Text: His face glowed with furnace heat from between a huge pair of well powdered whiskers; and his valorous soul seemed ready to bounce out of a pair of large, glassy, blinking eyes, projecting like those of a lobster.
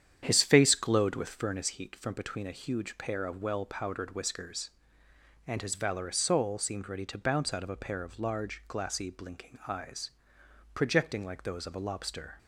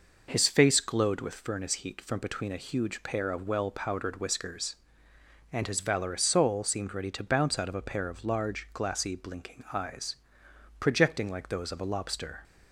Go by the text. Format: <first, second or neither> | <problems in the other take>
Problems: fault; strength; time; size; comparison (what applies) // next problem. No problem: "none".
second | starts louder than the rest; strong; until 1.7 s; 9 dB